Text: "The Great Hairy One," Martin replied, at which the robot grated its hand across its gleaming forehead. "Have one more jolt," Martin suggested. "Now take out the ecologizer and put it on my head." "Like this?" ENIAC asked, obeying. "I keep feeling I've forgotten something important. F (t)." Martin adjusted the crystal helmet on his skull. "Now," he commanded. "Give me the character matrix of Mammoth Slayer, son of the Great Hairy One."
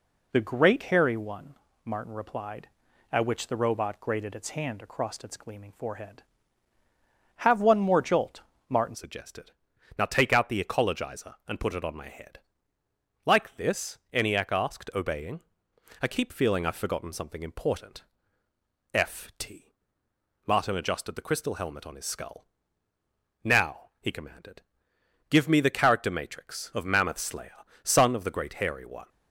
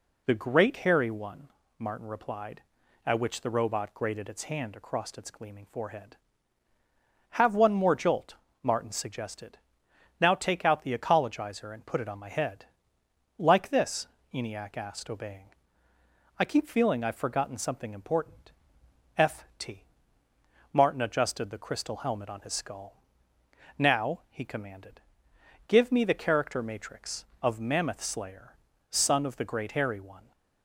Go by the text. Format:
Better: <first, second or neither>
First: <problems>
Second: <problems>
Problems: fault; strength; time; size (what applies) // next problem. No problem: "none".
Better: second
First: changes voice at "suggested"; from 8.9 s on; 20.1 s long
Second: none